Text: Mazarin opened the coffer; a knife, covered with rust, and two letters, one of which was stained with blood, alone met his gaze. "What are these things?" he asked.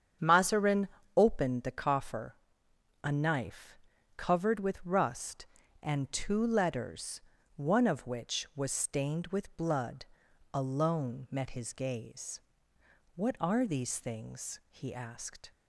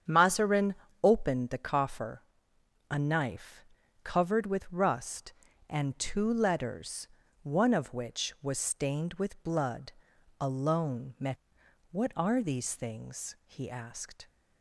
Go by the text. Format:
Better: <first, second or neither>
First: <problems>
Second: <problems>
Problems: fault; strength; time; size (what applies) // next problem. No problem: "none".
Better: first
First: starts louder than the rest; strong; until 1.4 s; 8.5 dB // pauses between "Mazarin" and "opened"; slight; at 0.8 s; 0.26 s long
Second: starts louder than the rest; strong; until 1.3 s; 8.5 dB // pauses between "Mazarin" and "opened"; slight; at 0.7 s; 0.26 s long // skips "his gaze"; at 11.6 s